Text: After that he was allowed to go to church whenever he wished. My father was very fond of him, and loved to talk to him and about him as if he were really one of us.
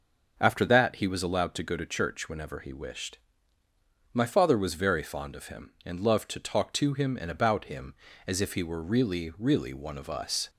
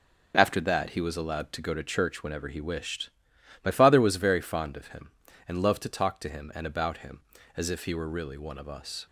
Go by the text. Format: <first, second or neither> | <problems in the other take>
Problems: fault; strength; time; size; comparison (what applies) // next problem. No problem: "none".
second | says "really" twice; at 9.3 s